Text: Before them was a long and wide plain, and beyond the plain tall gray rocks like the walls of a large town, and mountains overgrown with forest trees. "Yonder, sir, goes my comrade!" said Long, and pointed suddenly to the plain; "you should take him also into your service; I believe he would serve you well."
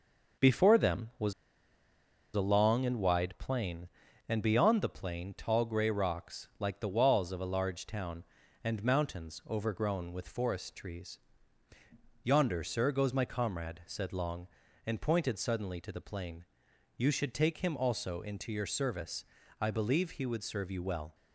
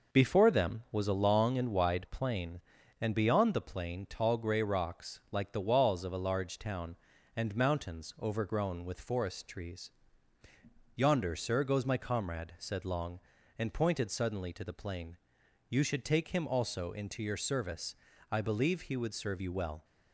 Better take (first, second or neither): second